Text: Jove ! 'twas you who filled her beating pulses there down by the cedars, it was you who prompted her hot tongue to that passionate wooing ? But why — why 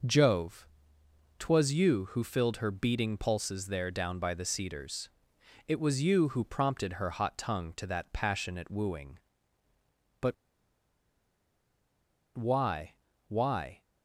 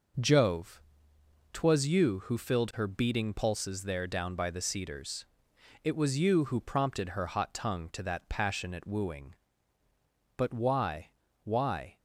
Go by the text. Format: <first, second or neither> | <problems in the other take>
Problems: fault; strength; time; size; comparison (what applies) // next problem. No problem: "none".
second | pauses between "But" and "why"; strong; at 10.3 s; 2.0 s long